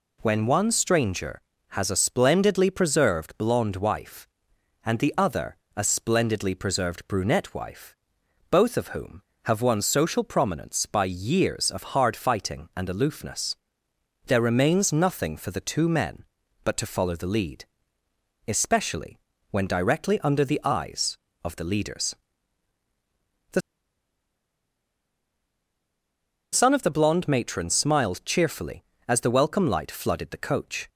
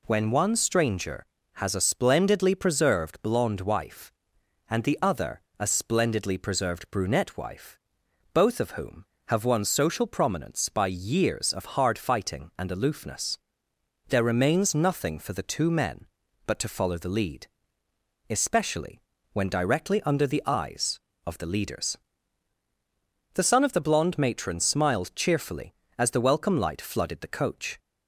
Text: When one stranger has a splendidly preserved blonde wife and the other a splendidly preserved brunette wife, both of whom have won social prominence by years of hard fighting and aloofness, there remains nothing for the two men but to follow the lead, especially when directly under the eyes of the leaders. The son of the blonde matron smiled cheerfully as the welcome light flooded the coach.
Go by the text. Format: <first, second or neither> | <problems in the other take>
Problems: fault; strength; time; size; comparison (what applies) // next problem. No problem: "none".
second | pauses between "other" and "a"; slight; at 5.5 s; 0.20 s long; slight in the second // pauses between "especially" and "when"; slight; at 19.2 s; 0.32 s long; slight in the second // pauses between "The" and "son"; strong; at 23.6 s; 2.9 s long